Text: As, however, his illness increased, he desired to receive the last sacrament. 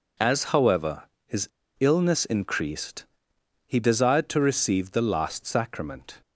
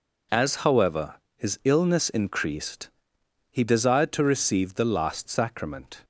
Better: second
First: pauses between "his" and "illness"; slight; at 1.4 s; 0.29 s long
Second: none

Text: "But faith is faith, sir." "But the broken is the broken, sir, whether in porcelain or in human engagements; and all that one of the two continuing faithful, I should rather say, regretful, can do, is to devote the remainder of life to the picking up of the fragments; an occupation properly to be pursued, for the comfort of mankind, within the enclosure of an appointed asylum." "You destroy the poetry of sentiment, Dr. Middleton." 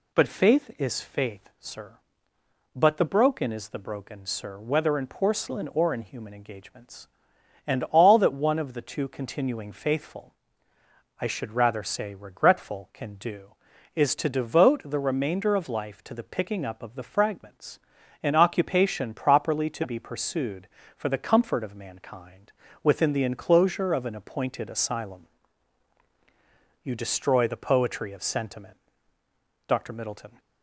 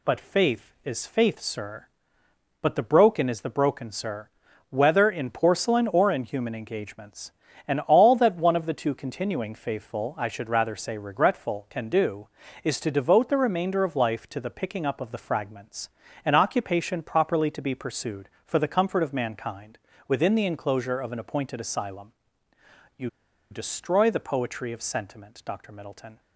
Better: first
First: none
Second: pauses between "You" and "destroy"; at 23.0 s; 0.42 s long

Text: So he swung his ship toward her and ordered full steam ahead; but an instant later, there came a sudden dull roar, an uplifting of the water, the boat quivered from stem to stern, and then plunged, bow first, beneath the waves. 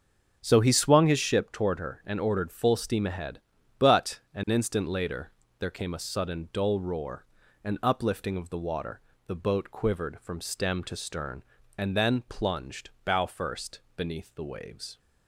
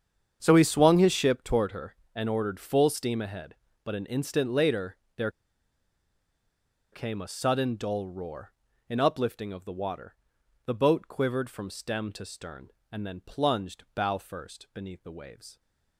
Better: first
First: starts louder than the rest; until 1.4 s; 6.5 dB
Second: starts louder than the rest; strong; until 1.4 s; 8 dB // pauses between "there" and "came"; strong; at 5.2 s; 1.6 s long

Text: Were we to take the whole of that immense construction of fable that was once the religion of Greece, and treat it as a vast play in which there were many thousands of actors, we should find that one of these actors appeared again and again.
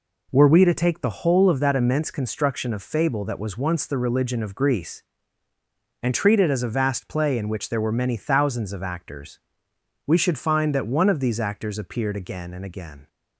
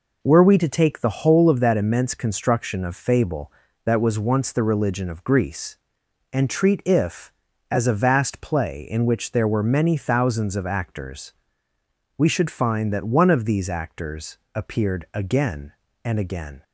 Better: first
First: none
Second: says "if" for "it"; at 6.8 s // pauses between "actors" and "appeared"; slight; at 14.3 s; 0.18 s long

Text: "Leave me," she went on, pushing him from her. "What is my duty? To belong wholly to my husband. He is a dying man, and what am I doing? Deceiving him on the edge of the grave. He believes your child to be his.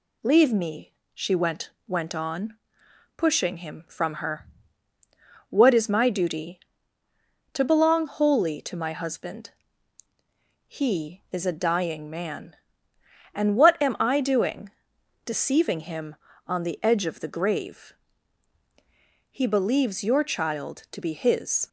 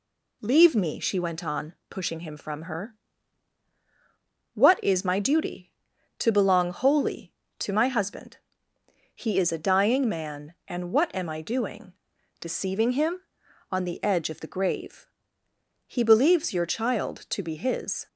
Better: second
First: says "went" twice; at 1.8 s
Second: none

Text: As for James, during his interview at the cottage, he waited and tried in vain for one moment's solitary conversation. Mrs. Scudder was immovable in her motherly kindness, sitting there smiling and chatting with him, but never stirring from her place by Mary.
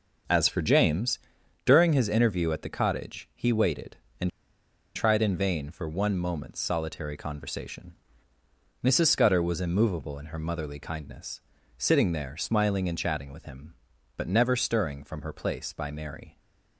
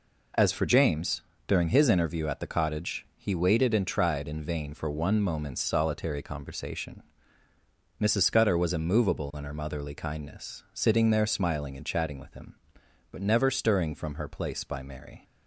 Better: second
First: starts louder than the rest; until 1.7 s; 6.5 dB // pauses between "and" and "tried"; noticeable; at 4.2 s; 0.65 s long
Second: none

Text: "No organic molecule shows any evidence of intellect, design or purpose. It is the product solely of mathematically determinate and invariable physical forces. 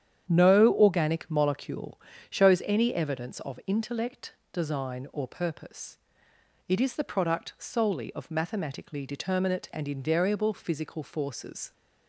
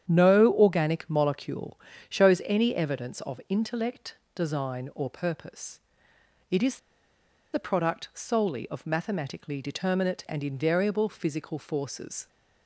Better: first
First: starts louder than the rest; strong; until 1.2 s; 9 dB // pauses between "molecule" and "shows"; slight; at 2.0 s; 0.28 s long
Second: starts louder than the rest; strong; until 1.0 s; 9 dB // pauses between "molecule" and "shows"; slight; at 1.8 s; 0.28 s long // pauses between "is" and "the"; noticeable; at 6.7 s; 0.76 s long

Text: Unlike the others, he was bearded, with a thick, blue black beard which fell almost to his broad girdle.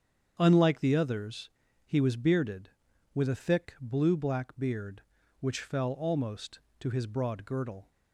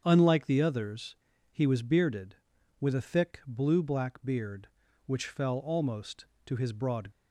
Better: first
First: starts louder than the rest; strong; until 1.3 s; 8 dB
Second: starts louder than the rest; strong; until 1.0 s; 7.5 dB // stops before "girdle"; at 7.1 s

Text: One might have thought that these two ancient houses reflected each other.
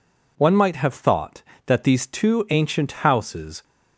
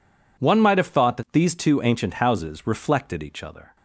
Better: second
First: stops before "reflected each other"; at 3.6 s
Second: none

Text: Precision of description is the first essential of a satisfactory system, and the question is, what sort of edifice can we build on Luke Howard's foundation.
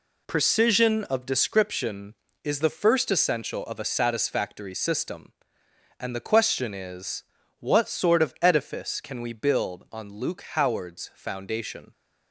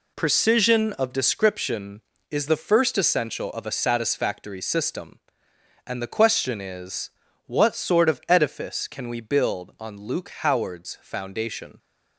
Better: neither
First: none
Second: none

